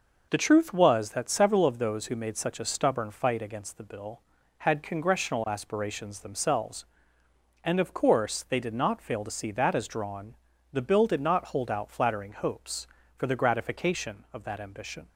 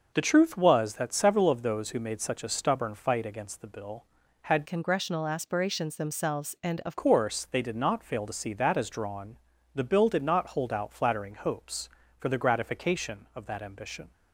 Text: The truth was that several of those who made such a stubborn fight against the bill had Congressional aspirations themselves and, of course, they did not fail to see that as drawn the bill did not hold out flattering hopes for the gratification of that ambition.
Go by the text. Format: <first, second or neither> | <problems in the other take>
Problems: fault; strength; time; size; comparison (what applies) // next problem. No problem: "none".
first | starts louder than the rest; noticeable; until 1.1 s; 6 dB // changes voice from "Congressional" to "of"; from 4.6 to 6.9 s; 2.3 s long // pauses between "drawn" and "the"; at 9.3 s; 0.38 s long; also in the first